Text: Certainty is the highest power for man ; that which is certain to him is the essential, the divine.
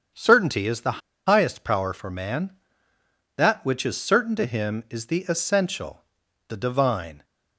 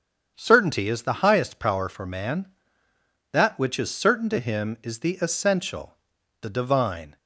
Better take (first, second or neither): second